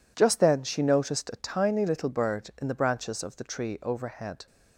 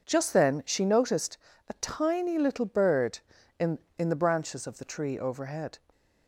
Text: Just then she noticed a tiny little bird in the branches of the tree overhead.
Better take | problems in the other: first | pauses between "noticed" and "a"; slight; at 1.3 s; 0.32 s long // says "in" twice; at 3.9 s

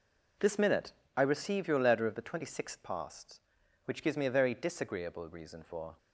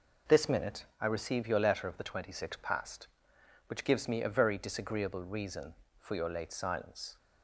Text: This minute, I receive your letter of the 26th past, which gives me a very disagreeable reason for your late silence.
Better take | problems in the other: second | stops before "your late silence"; at 5.9 s

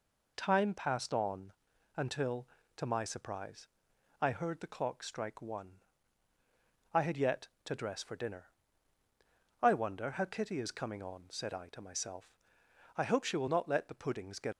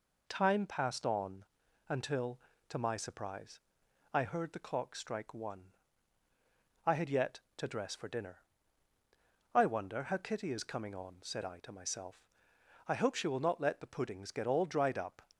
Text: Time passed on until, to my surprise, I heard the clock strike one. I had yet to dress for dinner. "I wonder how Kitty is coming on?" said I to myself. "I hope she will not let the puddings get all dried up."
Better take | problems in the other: second | pauses between "on" and "until"; at 1.5 s; 0.44 s long; also in the second // stops before "all dried up"; at 14.5 s

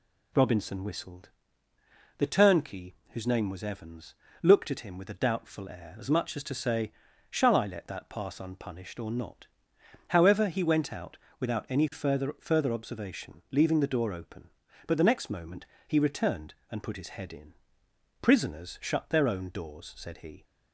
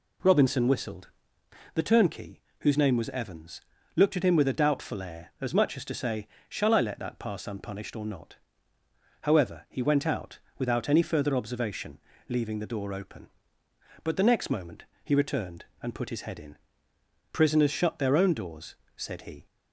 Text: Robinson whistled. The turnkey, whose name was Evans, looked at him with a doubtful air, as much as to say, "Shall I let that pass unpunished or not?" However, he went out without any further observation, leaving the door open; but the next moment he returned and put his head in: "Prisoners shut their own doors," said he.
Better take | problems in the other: second | pauses between "out" and "without"; slight; at 11.1 s; 0.22 s long; slight in the second // says "further" twice; at 12.3 s // pauses between "moment" and "he"; slight; at 15.6 s; 0.24 s long; slight in the second

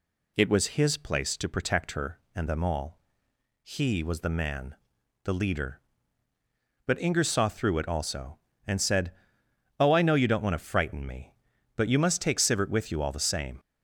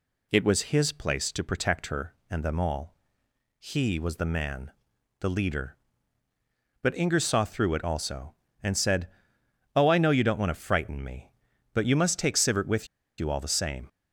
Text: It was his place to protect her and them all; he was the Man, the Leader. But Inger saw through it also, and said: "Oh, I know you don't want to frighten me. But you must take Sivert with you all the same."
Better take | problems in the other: first | pauses between "with" and "you"; slight; at 12.8 s; 0.31 s long

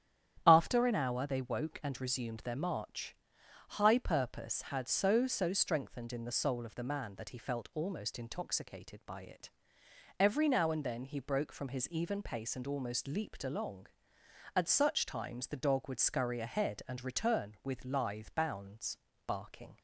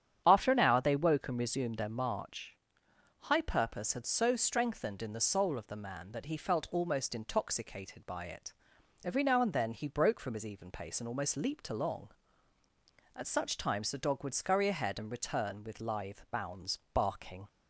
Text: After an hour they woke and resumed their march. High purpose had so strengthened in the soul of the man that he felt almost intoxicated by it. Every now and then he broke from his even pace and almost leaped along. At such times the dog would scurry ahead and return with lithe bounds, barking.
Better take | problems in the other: second | starts louder than the rest; strong; until 1.4 s; 10 dB; strong in the second // says "so" twice; at 5.2 s

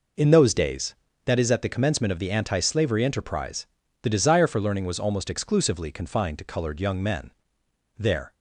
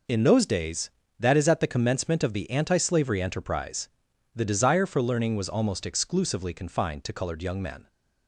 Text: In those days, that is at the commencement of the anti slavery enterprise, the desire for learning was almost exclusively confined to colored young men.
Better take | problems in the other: second | goes on to say "There"; slight; from 7.9 s on; 0.36 s long

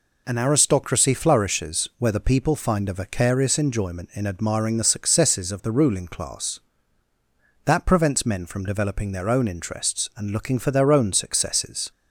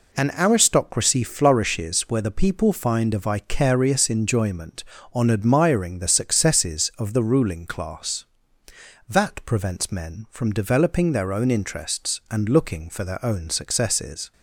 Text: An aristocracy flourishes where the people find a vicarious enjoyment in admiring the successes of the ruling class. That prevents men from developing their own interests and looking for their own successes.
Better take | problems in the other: first | says "on" for "in"; at 5.1 s

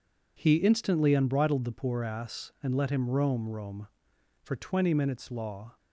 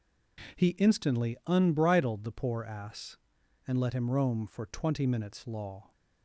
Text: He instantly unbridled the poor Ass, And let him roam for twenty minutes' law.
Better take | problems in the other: second | says "roam" twice; at 3.4 s

